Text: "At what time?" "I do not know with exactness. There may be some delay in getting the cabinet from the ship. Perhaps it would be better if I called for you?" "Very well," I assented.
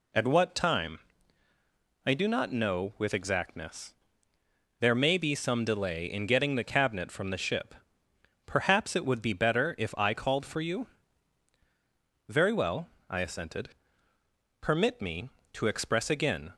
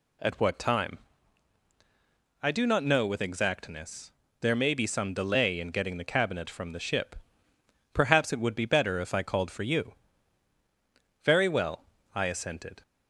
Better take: second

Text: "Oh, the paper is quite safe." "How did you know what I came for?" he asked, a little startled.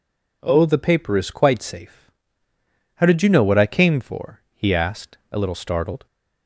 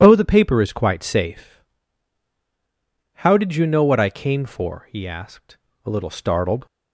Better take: neither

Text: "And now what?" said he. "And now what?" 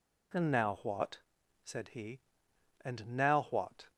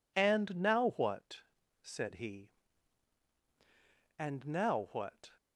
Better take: neither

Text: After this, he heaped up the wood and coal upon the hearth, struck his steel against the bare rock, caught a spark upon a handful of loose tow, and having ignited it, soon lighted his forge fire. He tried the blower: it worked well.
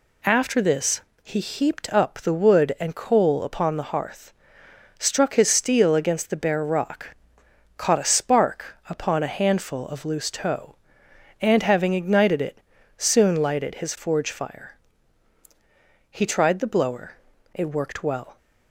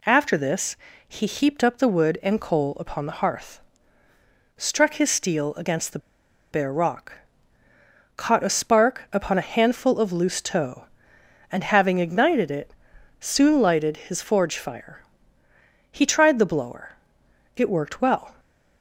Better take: first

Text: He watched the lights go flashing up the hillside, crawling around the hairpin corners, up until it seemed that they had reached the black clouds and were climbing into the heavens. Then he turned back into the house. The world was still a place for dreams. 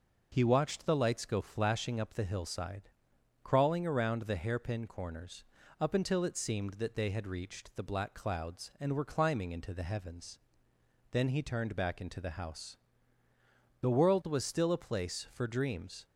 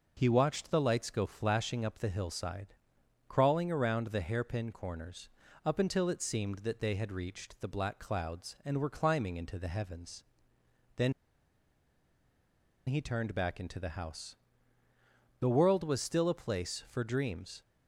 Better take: first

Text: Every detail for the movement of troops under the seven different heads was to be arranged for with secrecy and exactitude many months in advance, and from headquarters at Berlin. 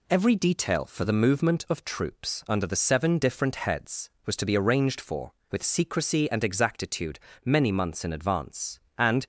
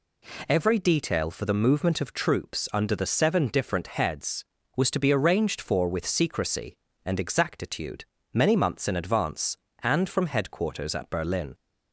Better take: second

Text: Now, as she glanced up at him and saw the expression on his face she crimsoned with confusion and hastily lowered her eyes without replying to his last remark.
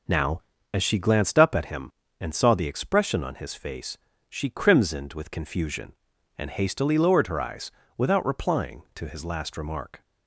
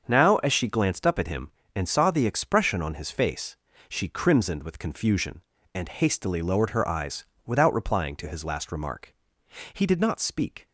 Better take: first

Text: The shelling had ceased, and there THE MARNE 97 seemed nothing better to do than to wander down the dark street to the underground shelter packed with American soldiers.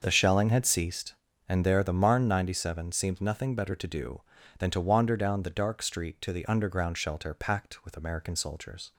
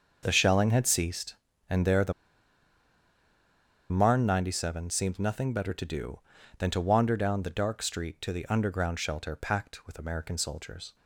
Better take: first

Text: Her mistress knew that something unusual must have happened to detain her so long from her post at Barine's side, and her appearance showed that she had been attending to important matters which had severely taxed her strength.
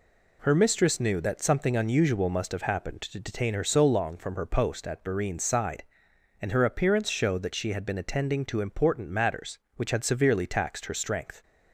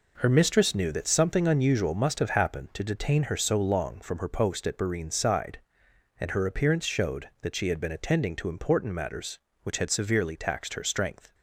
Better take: neither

